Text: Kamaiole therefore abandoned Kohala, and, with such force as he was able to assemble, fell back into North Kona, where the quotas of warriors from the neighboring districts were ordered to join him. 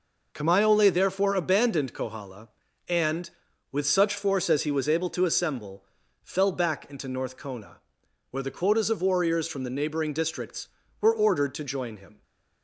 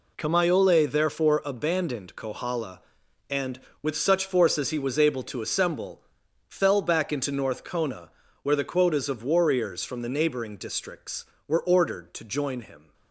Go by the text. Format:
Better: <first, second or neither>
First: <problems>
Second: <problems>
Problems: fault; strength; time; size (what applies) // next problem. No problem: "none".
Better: first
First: none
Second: gets quieter; strong; throughout; 9.5 dB